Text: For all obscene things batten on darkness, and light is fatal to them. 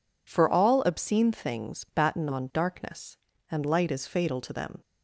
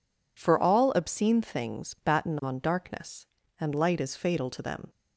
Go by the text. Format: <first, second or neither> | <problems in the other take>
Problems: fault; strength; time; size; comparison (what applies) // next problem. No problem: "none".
neither | none